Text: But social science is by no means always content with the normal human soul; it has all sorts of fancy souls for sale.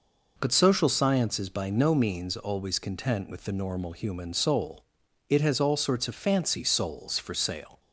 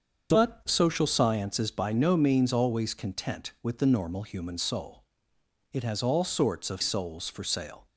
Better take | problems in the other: first | starts louder than the rest; until 1.3 s; 7 dB // skips "fancy"; at 6.7 s

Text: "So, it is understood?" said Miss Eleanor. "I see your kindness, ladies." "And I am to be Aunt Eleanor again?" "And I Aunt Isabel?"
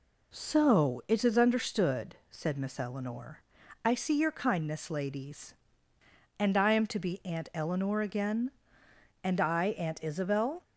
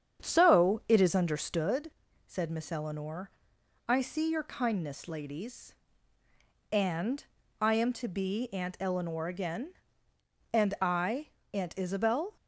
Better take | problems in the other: first | starts louder than the rest; strong; until 1.8 s; 8 dB // pauses between "And" and "I"; slight; at 7.2 s; 0.34 s long // pauses between "I" and "Aunt"; slight; at 11.2 s; 0.26 s long

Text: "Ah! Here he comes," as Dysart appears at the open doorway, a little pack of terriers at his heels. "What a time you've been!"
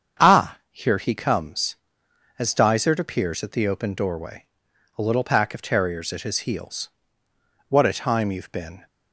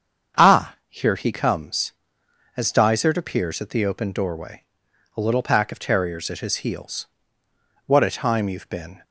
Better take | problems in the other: neither | starts louder than the rest; strong; the same in both

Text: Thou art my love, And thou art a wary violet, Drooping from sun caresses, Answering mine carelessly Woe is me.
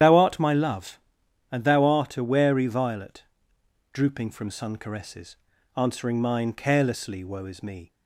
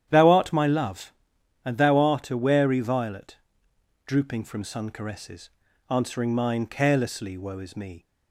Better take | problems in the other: second | loses the start of "Thou"; at 0.0 s; 45 ms // starts louder than the rest; strong; until 1.5 s; 10 dB; strong in the second

